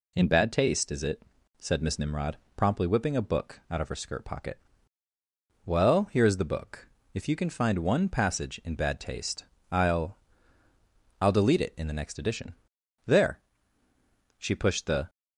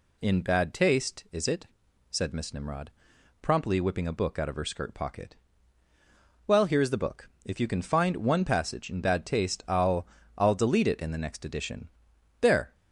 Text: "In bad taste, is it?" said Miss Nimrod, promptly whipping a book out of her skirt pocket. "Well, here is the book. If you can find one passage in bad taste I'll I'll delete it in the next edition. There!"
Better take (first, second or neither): second